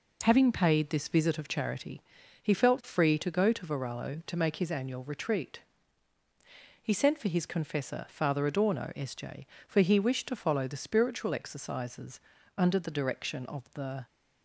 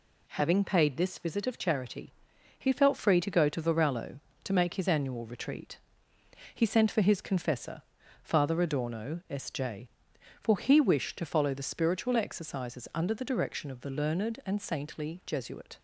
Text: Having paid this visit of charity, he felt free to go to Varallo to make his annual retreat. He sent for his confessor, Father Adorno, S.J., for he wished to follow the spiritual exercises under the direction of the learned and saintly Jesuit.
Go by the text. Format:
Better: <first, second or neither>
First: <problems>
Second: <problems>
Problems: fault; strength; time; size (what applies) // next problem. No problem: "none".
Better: second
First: pauses between "exercises" and "under"; slight; at 12.1 s; 0.36 s long // stops before "learned and saintly Jesuit"; at 14.0 s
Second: none